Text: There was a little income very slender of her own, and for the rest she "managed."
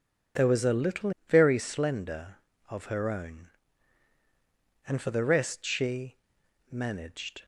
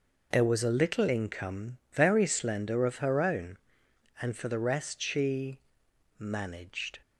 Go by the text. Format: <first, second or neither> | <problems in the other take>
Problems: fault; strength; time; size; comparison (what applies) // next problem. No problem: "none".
second | skips "income"; at 1.1 s // pauses between "she" and "managed"; noticeable; at 6.1 s; 0.56 s long; noticeable in the second